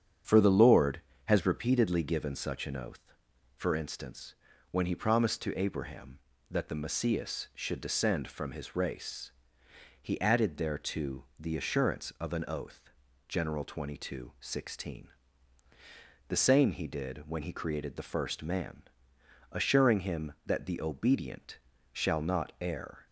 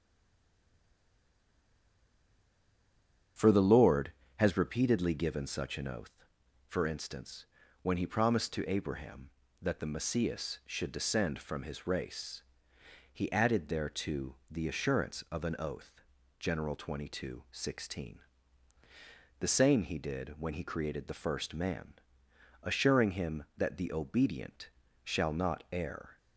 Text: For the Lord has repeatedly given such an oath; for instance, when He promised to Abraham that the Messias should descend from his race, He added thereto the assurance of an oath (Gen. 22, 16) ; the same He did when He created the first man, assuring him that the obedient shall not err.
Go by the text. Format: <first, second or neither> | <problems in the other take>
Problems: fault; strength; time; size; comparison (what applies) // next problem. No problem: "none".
first | stays silent before the first word; strong; until 3.3 s; 3.3 s long // starts louder than the rest; strong; until 4.6 s; 8 dB; strong in the first // pauses between "obedient" and "shall"; slight; at 24.7 s; 0.32 s long; slight in the first